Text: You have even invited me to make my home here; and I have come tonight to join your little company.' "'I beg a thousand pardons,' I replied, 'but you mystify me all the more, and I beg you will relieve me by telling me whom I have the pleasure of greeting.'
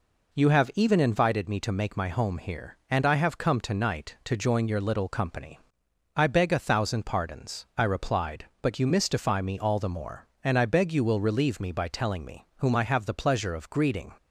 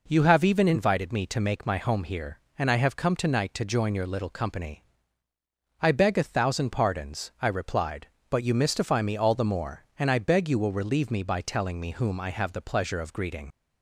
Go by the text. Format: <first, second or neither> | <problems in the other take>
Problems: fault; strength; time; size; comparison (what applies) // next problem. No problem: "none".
first | leaves "greeting" unfinished; at 13.5 s; 60 ms